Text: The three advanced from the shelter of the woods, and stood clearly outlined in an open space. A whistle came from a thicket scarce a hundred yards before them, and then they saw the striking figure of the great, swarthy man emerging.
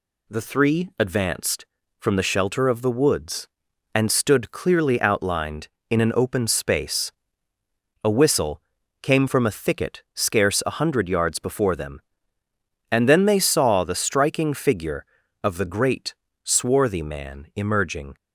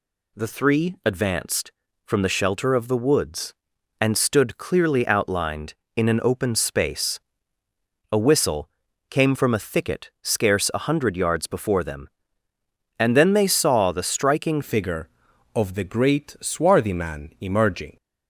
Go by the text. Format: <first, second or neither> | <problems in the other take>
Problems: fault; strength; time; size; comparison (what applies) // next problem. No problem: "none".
first | pauses between "whistle" and "came"; at 8.6 s; 0.40 s long; also in the first // changes voice at "figure"; from 14.6 s on; 3.3 s long